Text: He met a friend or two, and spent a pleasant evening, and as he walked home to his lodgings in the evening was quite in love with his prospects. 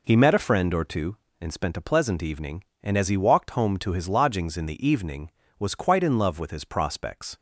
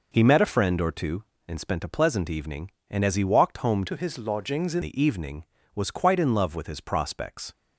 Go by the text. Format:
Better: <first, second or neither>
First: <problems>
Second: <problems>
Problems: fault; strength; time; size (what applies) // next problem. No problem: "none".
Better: first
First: none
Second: changes voice from "to" to "in"; from 3.8 to 4.8 s; 1.0 s long